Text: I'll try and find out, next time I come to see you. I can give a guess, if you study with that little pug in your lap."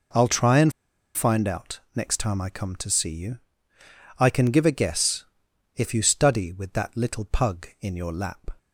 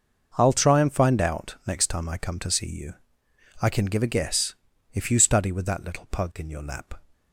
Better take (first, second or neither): second